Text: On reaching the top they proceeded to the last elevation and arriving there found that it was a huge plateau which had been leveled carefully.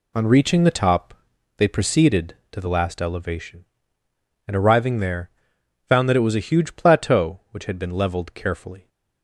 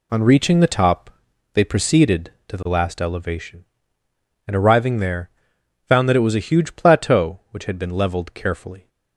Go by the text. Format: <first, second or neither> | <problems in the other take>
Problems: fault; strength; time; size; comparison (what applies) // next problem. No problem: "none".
neither | pauses between "top" and "they"; the same in both // pauses between "there" and "found"; noticeable; the same in both